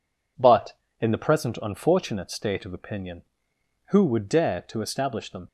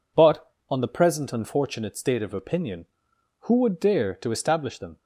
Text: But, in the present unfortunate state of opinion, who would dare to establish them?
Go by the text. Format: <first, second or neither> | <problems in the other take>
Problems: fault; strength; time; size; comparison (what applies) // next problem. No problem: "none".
first | says "on" for "in"; at 0.6 s